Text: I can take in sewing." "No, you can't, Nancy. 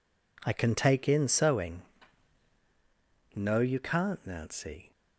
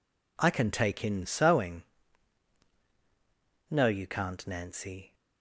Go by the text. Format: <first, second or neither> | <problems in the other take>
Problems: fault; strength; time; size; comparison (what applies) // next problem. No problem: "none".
neither | none